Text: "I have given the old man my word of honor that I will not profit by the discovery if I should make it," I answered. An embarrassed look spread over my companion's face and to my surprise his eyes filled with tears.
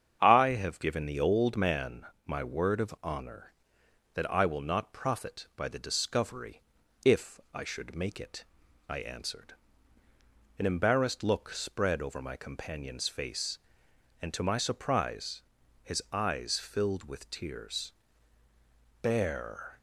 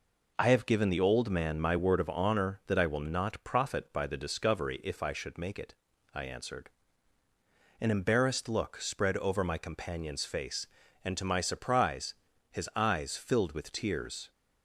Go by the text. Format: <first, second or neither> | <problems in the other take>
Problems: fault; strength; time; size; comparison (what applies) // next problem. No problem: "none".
second | starts louder than the rest; strong; until 1.2 s; 8 dB // pauses between "man" and "my"; slight; at 2.0 s; 0.22 s long // pauses between "discovery" and "if"; at 6.6 s; 0.44 s long // pauses between "surprise" and "his"; at 15.4 s; 0.40 s long; slight in the second // goes on to say "Bear"; noticeable; from 19.0 s on; 0.76 s long